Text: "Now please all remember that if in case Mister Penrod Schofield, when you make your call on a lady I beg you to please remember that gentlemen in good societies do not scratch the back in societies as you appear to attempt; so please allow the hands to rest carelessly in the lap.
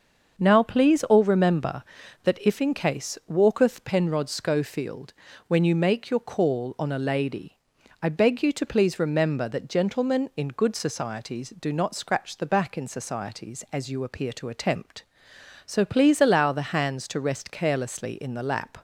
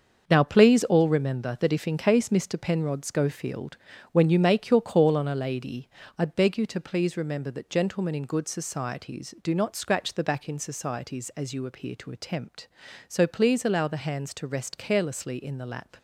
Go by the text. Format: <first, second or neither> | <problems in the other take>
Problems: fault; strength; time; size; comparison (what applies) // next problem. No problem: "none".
second | starts louder than the rest; until 1.4 s; 6.5 dB; also in the second // says "Walketh" for "Mister"; at 3.2 s // pauses between "lady" and "I"; noticeable; at 7.5 s; 0.46 s long; slight in the second